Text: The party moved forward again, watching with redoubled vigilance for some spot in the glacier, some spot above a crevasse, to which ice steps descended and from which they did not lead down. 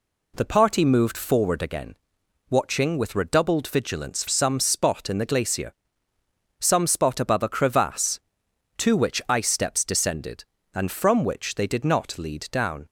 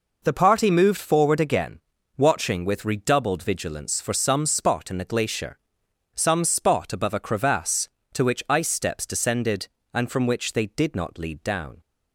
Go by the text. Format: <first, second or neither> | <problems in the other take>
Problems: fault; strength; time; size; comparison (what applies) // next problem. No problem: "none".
second | skips "for"; at 4.2 s